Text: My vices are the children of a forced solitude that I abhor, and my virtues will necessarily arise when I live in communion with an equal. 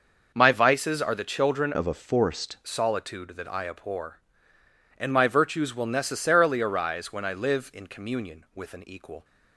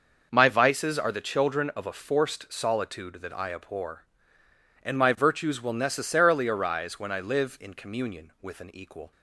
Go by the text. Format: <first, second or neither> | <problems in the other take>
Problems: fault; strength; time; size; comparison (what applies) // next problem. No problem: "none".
second | changes voice from "of" to "forced"; from 1.7 to 2.5 s; 0.8 s long